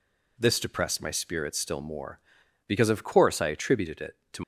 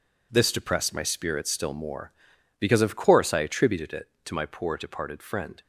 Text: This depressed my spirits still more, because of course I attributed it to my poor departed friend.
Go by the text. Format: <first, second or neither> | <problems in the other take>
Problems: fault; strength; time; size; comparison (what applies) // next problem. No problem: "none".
second | stops before "my poor departed friend"; at 4.4 s